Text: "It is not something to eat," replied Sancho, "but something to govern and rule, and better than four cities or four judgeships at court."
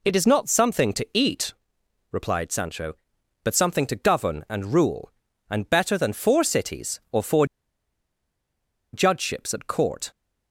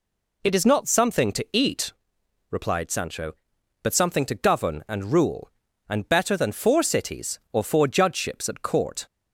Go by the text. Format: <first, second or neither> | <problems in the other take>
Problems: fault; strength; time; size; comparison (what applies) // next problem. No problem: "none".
second | pauses between "four" and "judgeships"; strong; at 7.4 s; 1.4 s long